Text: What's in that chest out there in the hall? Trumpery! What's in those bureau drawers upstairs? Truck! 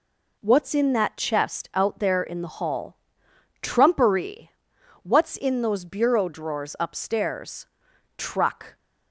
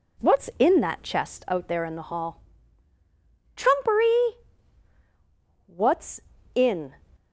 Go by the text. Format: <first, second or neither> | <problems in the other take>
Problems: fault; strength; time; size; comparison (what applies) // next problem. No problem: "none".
first | stops before "those bureau drawers upstairs Truck"; at 7.1 s